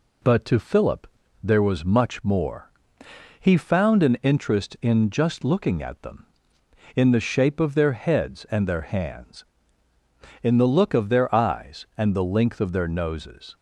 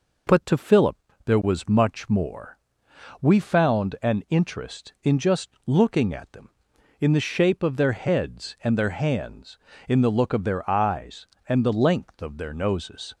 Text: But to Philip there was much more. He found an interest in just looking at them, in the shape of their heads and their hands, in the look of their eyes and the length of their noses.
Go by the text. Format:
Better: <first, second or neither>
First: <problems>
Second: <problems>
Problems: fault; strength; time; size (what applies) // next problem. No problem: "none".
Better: first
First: pauses between "Philip" and "there"; slight; at 1.0 s; 0.36 s long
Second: pauses between "Philip" and "there"; slight; at 0.9 s; 0.26 s long // says "We" for "He"; at 3.1 s // pauses between "just" and "looking"; slight; at 5.4 s; 0.16 s long